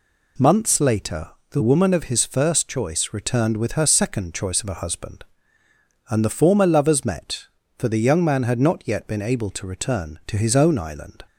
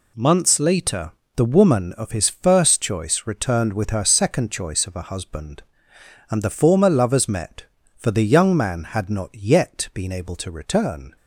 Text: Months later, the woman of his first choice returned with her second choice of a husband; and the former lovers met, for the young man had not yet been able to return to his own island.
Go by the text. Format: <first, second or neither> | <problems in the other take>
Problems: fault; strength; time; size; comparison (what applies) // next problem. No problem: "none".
first | stops before "to his own island"; at 11.1 s